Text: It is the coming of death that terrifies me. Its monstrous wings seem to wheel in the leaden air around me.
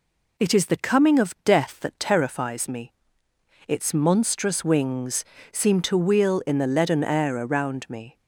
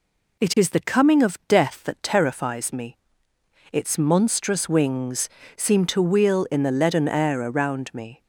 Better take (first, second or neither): neither